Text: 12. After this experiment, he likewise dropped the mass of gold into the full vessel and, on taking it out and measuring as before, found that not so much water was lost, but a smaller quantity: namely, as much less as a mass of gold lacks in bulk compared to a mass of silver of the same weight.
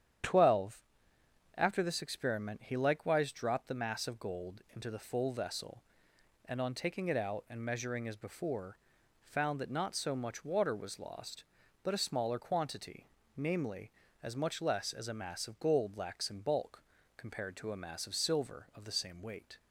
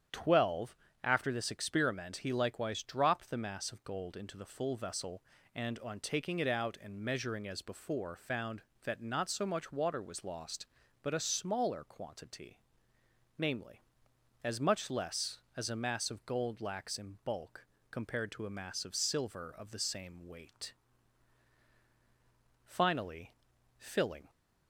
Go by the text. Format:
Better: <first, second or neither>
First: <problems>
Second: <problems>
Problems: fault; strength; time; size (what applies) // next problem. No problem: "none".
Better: first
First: starts louder than the rest; strong; until 1.9 s; 9.5 dB // pauses between "bulk" and "compared"; slight; at 16.8 s; 0.34 s long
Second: starts louder than the rest; strong; until 1.4 s; 9 dB // pauses between "bulk" and "compared"; slight; at 17.6 s; 0.26 s long // goes on to say "Finally filling"; from 22.6 s on; 1.6 s long